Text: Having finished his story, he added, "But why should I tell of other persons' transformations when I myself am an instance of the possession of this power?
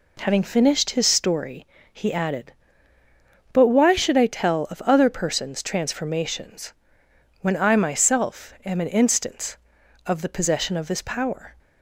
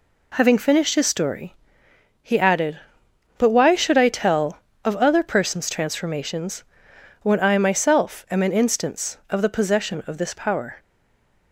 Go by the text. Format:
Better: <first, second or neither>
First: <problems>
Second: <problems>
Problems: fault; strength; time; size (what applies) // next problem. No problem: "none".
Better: first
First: pauses between "transformations" and "when"; noticeable; at 6.7 s; 0.68 s long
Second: pauses between "transformations" and "when"; noticeable; at 6.6 s; 0.58 s long // stays silent after the last word; slight; from 10.7 s on; 0.8 s long